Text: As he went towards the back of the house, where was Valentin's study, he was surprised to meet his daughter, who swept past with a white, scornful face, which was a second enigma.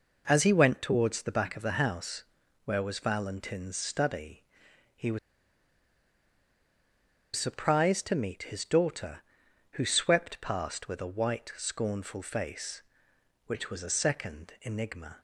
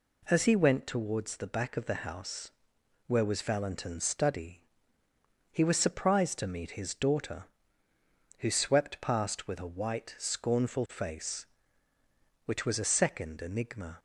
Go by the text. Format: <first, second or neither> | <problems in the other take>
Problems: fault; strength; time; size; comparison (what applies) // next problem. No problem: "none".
second | pauses between "was" and "surprised"; strong; at 5.1 s; 2.1 s long